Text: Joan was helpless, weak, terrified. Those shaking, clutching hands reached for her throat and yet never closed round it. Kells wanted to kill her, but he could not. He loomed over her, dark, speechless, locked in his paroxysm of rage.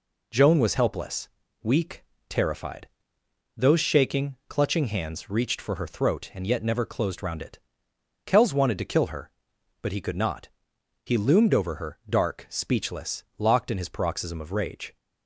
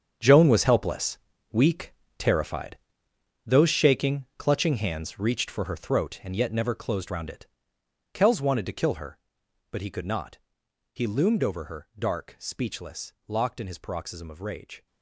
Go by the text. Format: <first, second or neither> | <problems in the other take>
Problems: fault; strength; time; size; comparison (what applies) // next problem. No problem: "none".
first | gets quieter; strong; throughout; 13 dB